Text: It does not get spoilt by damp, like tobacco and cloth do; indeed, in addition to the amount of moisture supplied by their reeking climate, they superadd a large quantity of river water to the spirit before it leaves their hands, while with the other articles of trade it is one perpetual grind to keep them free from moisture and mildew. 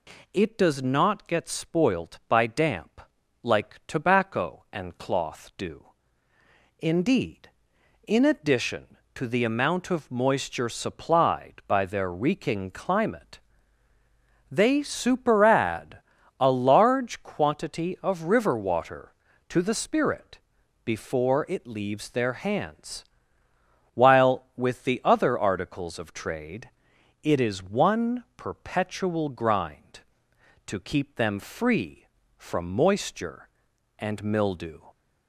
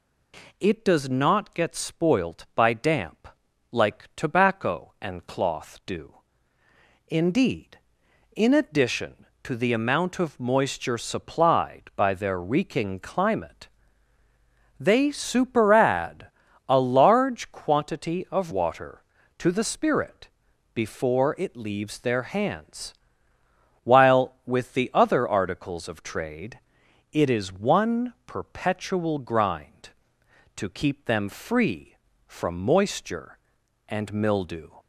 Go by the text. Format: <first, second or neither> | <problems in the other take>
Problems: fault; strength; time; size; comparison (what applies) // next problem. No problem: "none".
first | pauses between "superadd" and "a"; at 16.2 s; 0.44 s long; also in the first // skips "river"; at 18.5 s // pauses between "spirit" and "before"; noticeable; at 20.2 s; 0.46 s long; noticeable in the first // pauses between "trade" and "it"; noticeable; at 26.5 s; 0.54 s long; noticeable in the first